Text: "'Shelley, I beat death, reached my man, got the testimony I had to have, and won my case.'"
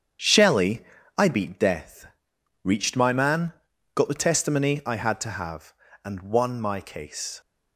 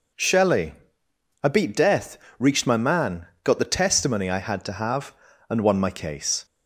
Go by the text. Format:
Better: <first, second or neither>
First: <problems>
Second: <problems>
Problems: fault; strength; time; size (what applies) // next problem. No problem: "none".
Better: second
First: gets quieter; strong; throughout; 8.5 dB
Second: none